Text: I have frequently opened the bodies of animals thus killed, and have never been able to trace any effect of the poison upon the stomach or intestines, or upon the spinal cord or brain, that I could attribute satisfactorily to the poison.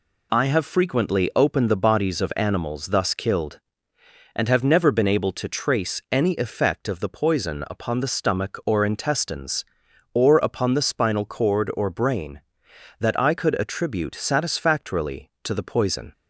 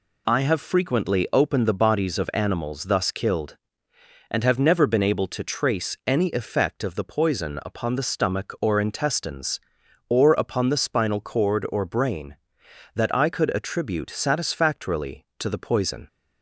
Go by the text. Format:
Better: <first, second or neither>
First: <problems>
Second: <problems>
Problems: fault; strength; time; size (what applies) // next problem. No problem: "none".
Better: neither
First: none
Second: none